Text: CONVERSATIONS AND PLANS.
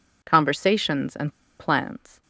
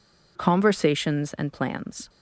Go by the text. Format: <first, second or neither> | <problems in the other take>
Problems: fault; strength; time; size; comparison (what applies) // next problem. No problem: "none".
second | pauses between "AND" and "PLANS"; slight; at 1.3 s; 0.27 s long